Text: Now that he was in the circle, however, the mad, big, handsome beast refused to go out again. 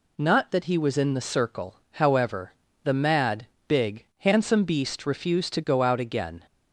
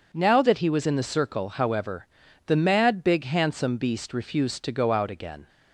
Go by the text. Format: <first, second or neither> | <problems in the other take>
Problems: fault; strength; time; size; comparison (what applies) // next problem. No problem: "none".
second | says "Not" for "Now"; at 0.1 s